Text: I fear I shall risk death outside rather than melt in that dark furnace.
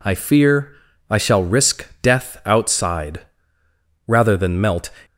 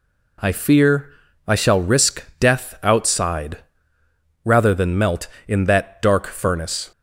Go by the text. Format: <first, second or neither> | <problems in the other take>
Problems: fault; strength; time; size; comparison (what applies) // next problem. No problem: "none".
second | pauses between "fear" and "I"; slight; at 0.7 s; 0.36 s long; slight in the second // pauses between "risk" and "death"; slight; at 1.8 s; 0.16 s long; slight in the second // pauses between "outside" and "rather"; noticeable; at 3.1 s; 0.88 s long; noticeable in the second // stops before "in that dark furnace"; at 5.0 s